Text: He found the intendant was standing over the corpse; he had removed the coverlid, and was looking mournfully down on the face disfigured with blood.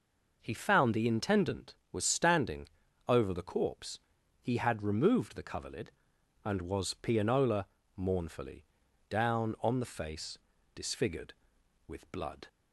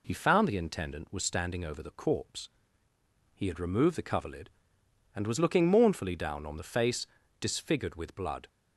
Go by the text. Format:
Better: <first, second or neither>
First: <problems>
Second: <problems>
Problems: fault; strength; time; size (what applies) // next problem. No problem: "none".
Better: second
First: pauses between "standing" and "over"; at 2.6 s; 0.40 s long // says "pianola" for "looking"; at 6.9 s // pauses between "mournfully" and "down"; noticeable; at 8.6 s; 0.46 s long // pauses between "face" and "disfigured"; slight; at 10.3 s; 0.34 s long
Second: pauses between "face" and "disfigured"; slight; at 7.0 s; 0.32 s long